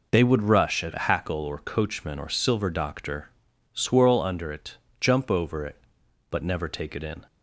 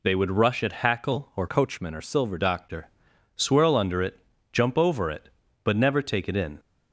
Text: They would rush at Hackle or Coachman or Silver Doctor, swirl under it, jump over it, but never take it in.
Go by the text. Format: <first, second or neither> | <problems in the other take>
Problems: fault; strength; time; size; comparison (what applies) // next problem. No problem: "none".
first | changes voice from "Coachman" to "Silver"; from 1.4 to 2.3 s; 0.9 s long